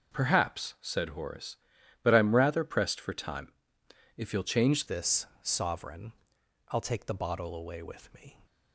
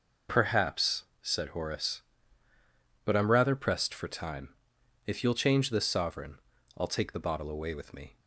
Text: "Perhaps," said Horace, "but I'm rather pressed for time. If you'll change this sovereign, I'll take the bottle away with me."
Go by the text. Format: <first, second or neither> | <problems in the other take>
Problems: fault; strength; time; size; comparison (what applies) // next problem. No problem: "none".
second | changes voice at "this"; from 4.8 s on; 3.5 s long // pauses between "this" and "sovereign"; slight; at 5.2 s; 0.16 s long